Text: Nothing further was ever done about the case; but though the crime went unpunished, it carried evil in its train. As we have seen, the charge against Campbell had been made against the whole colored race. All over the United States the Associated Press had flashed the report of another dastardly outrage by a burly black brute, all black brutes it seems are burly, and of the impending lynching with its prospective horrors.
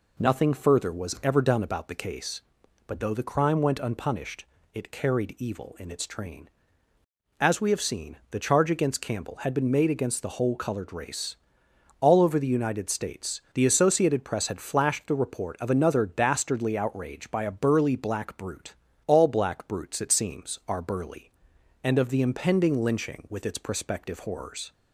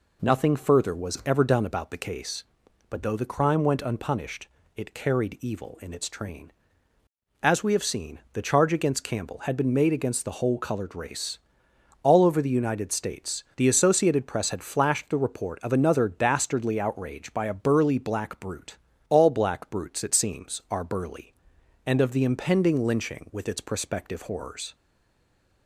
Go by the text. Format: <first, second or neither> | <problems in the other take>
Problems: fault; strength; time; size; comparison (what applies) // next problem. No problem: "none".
first | stays silent after the last word; slight; from 24.7 s on; 0.9 s long